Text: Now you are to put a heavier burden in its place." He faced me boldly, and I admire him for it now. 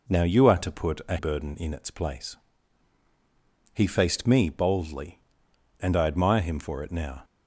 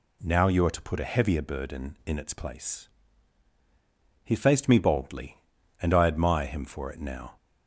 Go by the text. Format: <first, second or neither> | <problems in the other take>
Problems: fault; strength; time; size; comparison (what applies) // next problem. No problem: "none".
second | skips "heavier"; at 1.1 s